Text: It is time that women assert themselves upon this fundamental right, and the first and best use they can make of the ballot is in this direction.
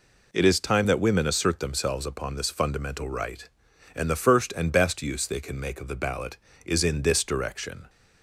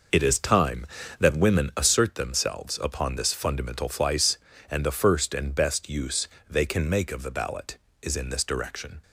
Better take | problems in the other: first | says "flice" for "right"; at 3.8 s // pauses between "use" and "they"; slight; at 6.2 s; 0.24 s long

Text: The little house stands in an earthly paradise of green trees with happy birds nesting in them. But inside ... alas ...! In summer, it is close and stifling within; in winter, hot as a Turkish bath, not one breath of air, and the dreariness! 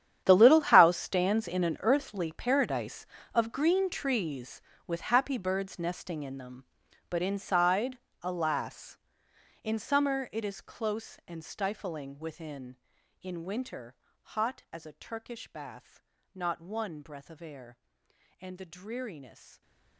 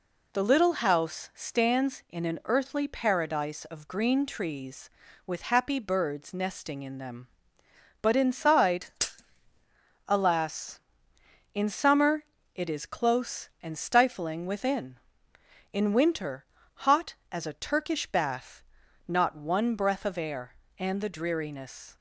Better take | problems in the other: second | gets quieter; strong; throughout; 16.5 dB

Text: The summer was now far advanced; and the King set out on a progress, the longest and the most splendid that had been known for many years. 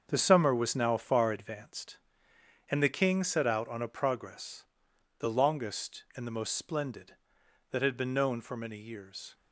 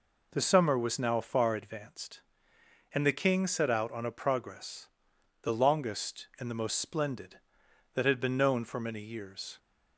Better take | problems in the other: second | gets quieter; strong; throughout; 9.5 dB

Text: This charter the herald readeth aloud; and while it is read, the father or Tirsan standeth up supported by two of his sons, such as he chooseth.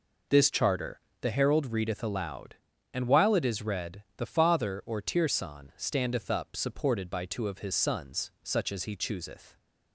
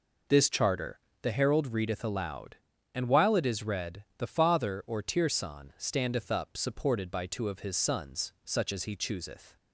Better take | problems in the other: neither | pauses between "charter" and "the"; slight; the same in both

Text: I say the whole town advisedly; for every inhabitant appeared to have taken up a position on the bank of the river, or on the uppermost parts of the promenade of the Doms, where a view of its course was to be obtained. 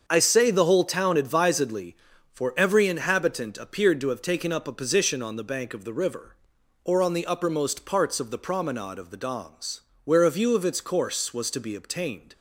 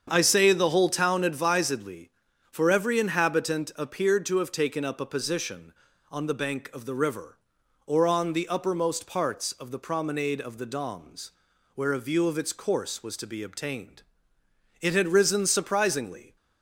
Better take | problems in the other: first | starts louder than the rest; strong; until 1.1 s; 7.5 dB; also in the first // goes on to say "It had risen surprisingly"; from 14.7 s on; 1.5 s long

